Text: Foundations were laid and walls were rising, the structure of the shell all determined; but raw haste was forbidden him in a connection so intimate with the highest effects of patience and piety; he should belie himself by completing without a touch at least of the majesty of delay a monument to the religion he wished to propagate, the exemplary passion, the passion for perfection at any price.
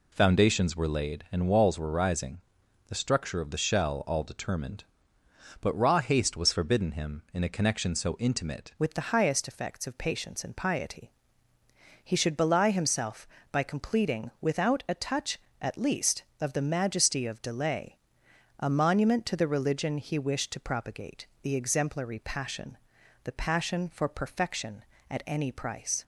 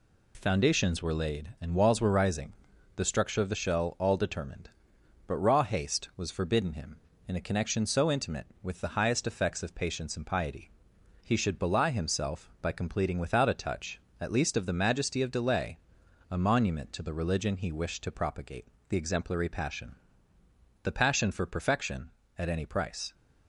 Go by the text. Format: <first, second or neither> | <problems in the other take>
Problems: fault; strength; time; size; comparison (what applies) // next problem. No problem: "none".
second | changes voice at "with"; from 8.7 s on; 17.3 s long // pauses between "delay" and "a"; noticeable; at 17.9 s; 0.64 s long; noticeable in the second